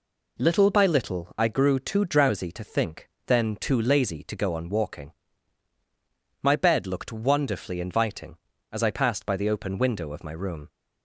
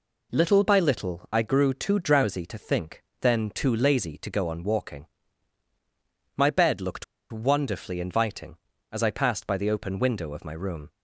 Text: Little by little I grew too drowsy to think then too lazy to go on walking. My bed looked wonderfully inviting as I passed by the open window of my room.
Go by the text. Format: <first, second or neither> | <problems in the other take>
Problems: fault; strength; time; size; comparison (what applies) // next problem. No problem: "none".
first | pauses between "think" and "then"; slight; at 3.0 s; 0.20 s long; slight in the first // pauses between "looked" and "wonderfully"; slight; at 7.0 s; 0.26 s long